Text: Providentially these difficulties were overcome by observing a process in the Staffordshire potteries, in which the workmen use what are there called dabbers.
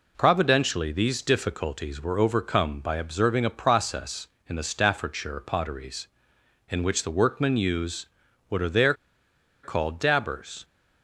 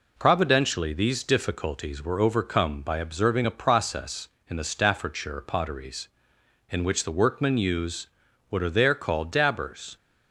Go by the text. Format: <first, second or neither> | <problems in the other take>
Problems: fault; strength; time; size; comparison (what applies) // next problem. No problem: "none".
second | pauses between "use" and "what"; at 8.0 s; 0.40 s long; also in the second // pauses between "there" and "called"; noticeable; at 8.9 s; 0.70 s long